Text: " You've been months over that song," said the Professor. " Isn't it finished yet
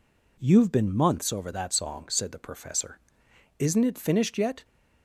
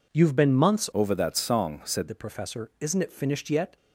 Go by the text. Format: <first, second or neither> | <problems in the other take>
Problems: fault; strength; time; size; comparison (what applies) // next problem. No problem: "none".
first | changes voice from "over" to "said"; from 0.9 to 2.0 s; 1.1 s long